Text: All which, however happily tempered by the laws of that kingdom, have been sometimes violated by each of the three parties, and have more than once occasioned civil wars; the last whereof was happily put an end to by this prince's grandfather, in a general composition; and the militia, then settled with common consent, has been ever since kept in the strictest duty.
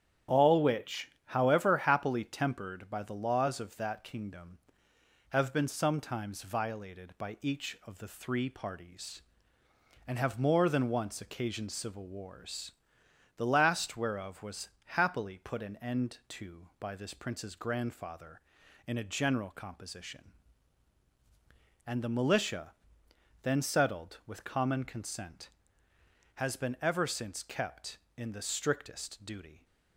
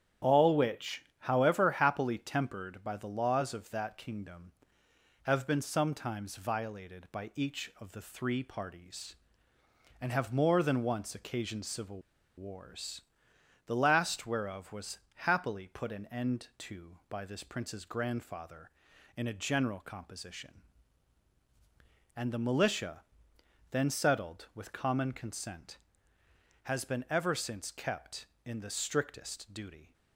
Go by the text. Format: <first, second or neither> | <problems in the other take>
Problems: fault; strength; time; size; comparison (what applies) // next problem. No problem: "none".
first | starts louder than the rest; strong; until 1.3 s; 9.5 dB; strong in the first // pauses between "civil" and "wars"; at 11.9 s; 0.38 s long // pauses between "was" and "happily"; slight; at 14.9 s; 0.32 s long; slight in the first